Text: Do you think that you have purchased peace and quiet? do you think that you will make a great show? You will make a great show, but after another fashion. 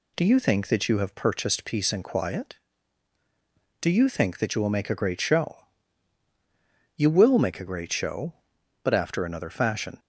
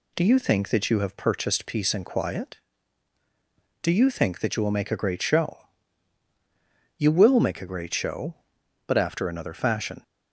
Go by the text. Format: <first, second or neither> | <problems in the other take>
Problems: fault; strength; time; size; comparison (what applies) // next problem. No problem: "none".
neither | none